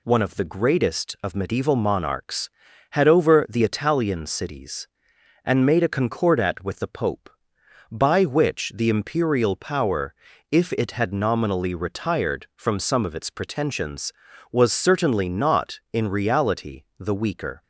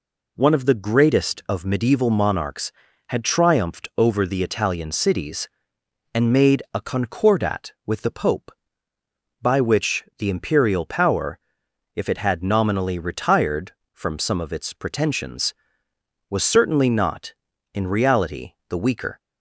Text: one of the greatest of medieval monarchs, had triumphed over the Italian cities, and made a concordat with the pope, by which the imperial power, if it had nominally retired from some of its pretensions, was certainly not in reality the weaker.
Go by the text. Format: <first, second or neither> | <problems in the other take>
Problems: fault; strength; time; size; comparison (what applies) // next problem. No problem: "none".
second | skips "triumphed"; at 3.0 s // pauses between "reality" and "the"; slight; at 16.8 s; 0.16 s long; slight in the second